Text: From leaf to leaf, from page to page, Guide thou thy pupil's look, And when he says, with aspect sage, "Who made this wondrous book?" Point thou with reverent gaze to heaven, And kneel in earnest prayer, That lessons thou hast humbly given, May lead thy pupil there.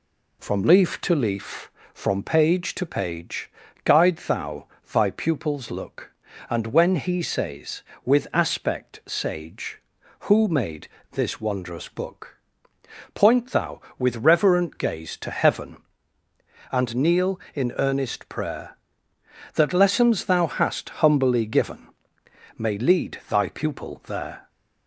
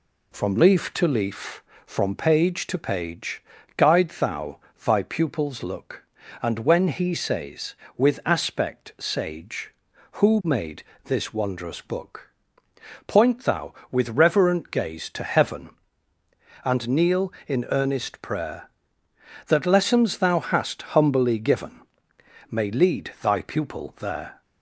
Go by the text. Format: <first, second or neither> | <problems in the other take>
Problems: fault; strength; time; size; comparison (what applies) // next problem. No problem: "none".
neither | pauses between "thou" and "thy"; slight; the same in both // pauses between "made" and "this"; slight; the same in both